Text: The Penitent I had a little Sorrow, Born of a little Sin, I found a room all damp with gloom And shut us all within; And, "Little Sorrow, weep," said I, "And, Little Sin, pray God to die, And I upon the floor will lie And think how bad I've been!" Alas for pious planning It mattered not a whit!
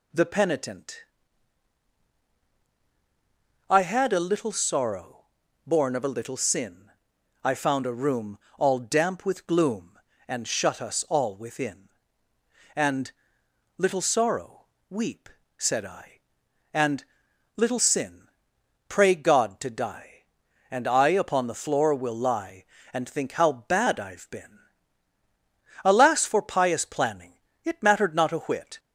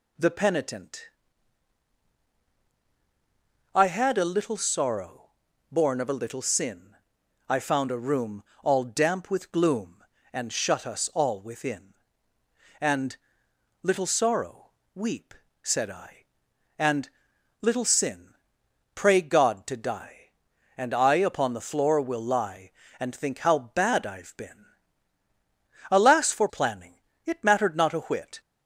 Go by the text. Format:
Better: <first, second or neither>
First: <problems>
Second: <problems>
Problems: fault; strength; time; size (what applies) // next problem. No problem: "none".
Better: first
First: pauses between "Penitent" and "I"; strong; at 1.0 s; 2.6 s long // pauses between "room" and "all"; slight; at 8.3 s; 0.20 s long // pauses between "planning" and "It"; slight; at 27.3 s; 0.26 s long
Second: pauses between "Penitent" and "I"; strong; at 1.0 s; 2.6 s long // pauses between "room" and "all"; slight; at 8.4 s; 0.20 s long // skips "pious"; at 26.4 s // pauses between "planning" and "It"; slight; at 27.0 s; 0.26 s long